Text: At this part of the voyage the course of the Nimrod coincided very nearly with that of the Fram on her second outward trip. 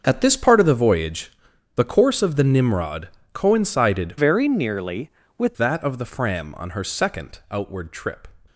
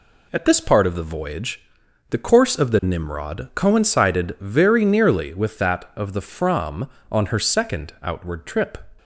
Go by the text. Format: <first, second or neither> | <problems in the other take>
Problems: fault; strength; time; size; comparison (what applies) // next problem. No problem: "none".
second | starts louder than the rest; until 1.0 s; 6.5 dB // pauses between "voyage" and "the"; noticeable; at 1.3 s; 0.46 s long; noticeable in the second // pauses between "Nimrod" and "coincided"; slight; at 3.0 s; 0.24 s long // changes voice from "very" to "with"; from 4.1 to 5.5 s; 1.4 s long